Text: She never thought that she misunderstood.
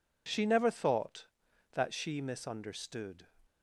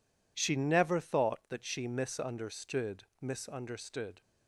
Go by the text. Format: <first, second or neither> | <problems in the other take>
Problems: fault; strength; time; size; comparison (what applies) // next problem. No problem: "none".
first | says "misunderstood" twice; at 3.2 s